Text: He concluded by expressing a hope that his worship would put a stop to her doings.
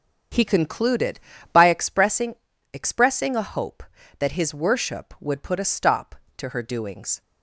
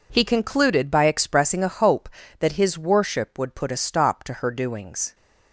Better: second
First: starts louder than the rest; strong; until 1.6 s; 7.5 dB // says "expressing" twice; at 2.7 s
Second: none

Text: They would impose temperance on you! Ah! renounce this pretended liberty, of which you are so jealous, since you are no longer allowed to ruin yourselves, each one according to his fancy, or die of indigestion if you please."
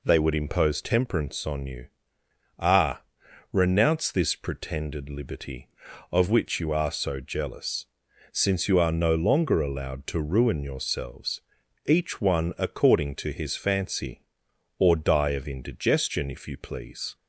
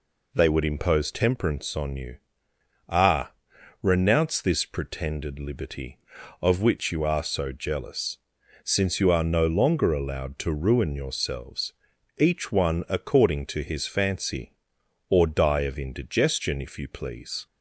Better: neither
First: none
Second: none

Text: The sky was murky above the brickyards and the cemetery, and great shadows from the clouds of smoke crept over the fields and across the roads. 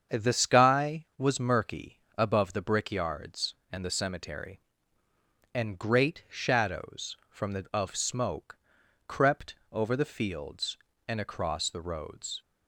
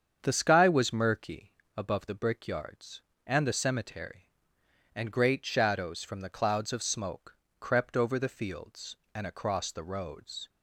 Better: second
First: starts louder than the rest; strong; until 1.2 s; 7.5 dB // pauses between "murky" and "above"; slight; at 1.9 s; 0.18 s long // skips "clouds"; at 7.7 s // pauses between "smoke" and "crept"; noticeable; at 8.5 s; 0.50 s long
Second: starts louder than the rest; strong; until 1.2 s; 7.5 dB // pauses between "murky" and "above"; slight; at 1.5 s; 0.24 s long // pauses between "smoke" and "crept"; slight; at 7.3 s; 0.22 s long

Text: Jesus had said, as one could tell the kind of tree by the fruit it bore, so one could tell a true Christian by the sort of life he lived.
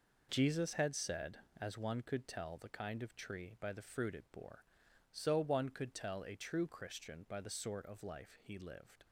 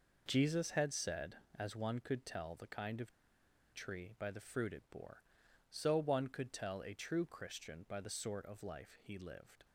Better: first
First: none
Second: pauses between "of" and "tree"; noticeable; at 3.1 s; 0.61 s long

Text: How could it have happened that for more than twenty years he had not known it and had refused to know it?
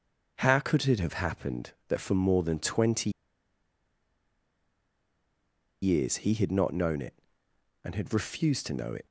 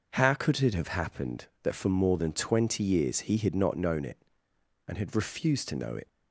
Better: second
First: starts louder than the rest; noticeable; until 1.4 s; 6 dB // pauses between "twenty" and "years"; strong; at 3.0 s; 2.7 s long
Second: none

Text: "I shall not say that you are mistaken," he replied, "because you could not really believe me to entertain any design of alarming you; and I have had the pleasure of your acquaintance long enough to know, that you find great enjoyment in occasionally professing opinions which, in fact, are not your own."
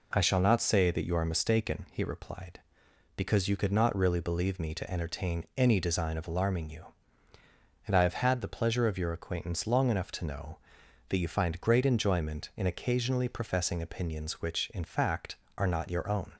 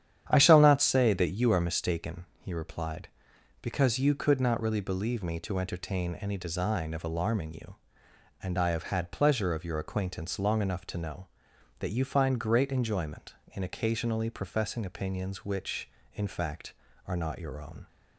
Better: first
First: none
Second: starts louder than the rest; strong; until 1.2 s; 9.5 dB // skips "the"; at 9.1 s

